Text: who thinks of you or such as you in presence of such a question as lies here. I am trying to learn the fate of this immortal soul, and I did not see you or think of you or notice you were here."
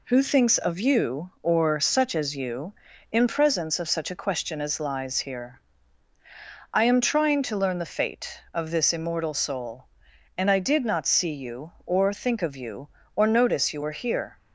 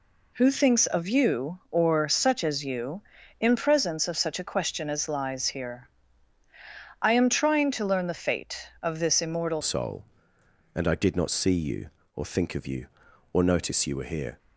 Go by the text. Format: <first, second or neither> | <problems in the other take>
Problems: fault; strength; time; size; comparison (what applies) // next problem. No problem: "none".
first | changes voice at "soul"; from 9.6 s on; 4.7 s long